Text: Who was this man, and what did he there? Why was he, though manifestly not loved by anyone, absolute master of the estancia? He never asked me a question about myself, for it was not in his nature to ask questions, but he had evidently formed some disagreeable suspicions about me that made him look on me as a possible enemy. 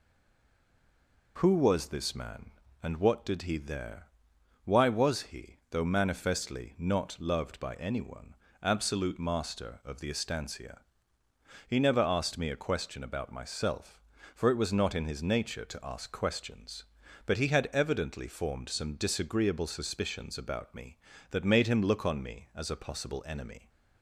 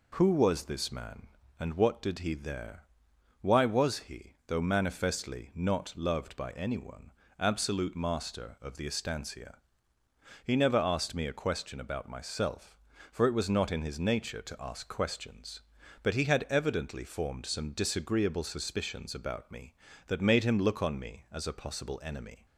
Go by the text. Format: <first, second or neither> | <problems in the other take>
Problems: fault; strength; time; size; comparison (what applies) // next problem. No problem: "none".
second | stays silent before the first word; noticeable; until 1.3 s; 1.3 s long